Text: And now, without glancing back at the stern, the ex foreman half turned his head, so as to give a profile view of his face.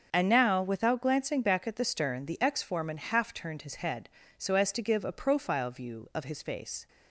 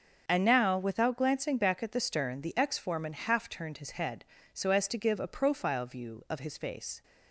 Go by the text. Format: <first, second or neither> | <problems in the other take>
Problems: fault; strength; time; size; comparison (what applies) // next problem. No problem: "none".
neither | starts louder than the rest; the same in both